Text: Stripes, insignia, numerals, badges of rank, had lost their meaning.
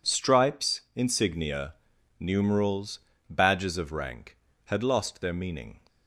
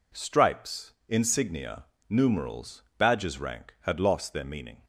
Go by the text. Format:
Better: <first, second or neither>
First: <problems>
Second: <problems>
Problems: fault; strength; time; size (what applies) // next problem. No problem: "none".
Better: first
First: none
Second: skips "of"; at 3.4 s